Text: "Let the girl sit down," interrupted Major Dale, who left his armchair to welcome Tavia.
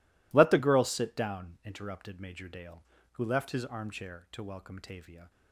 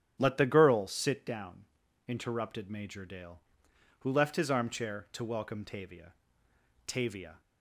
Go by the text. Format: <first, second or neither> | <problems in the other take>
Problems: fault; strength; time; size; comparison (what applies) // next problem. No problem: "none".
first | starts louder than the rest; strong; until 1.2 s; 10 dB // says "Tavia" twice; at 6.8 s